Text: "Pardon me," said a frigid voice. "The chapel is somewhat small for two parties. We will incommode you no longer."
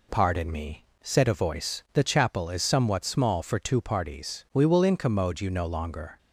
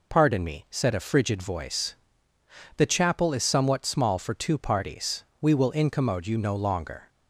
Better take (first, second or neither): second